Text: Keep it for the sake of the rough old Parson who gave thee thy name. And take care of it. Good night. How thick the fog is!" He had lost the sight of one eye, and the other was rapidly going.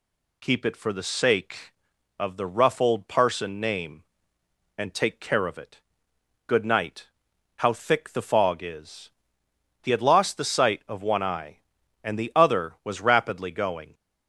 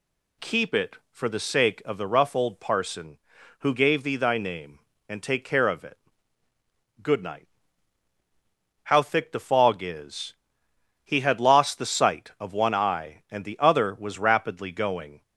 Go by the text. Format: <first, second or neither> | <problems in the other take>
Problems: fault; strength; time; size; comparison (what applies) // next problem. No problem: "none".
second | skips "who gave thee thy"; at 3.5 s